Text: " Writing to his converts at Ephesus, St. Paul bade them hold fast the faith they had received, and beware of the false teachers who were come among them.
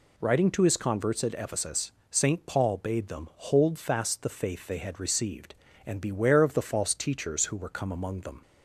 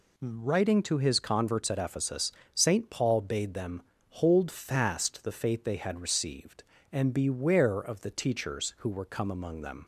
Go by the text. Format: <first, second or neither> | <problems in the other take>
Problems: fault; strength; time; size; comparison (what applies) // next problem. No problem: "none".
first | pauses between "them" and "hold"; slight; at 3.8 s; 0.26 s long // skips "false"; at 8.0 s